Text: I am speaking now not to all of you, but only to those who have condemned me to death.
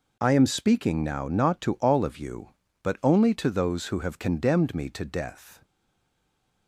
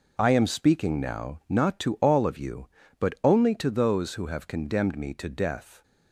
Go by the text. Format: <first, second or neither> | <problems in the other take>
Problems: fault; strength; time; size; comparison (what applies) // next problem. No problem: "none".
second | stays silent after the last word; from 5.6 s on; 1.0 s long